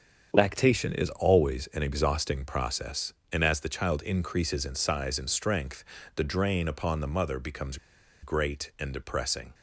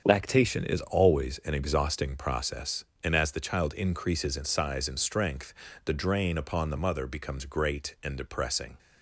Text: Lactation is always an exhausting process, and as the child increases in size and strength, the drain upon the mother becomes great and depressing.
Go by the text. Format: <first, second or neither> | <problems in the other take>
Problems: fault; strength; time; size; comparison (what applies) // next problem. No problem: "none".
second | starts louder than the rest; until 1.3 s; 7 dB; also in the second // pauses between "becomes" and "great"; noticeable; at 7.7 s; 0.46 s long